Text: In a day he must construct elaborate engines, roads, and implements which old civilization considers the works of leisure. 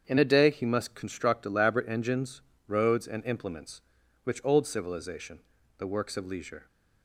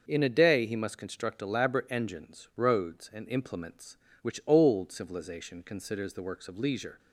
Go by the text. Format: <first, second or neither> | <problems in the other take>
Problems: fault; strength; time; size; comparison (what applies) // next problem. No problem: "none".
second | starts louder than the rest; strong; until 1.0 s; 7.5 dB; noticeable in the second // skips "considers"; at 5.5 s